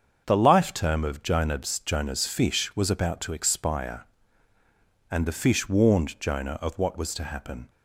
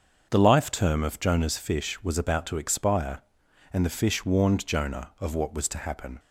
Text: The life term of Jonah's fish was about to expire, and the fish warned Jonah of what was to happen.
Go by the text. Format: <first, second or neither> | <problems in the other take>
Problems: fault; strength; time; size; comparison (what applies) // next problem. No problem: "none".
second | starts louder than the rest; until 1.2 s; 7 dB; also in the second // says "Jonah's" twice; at 1.7 s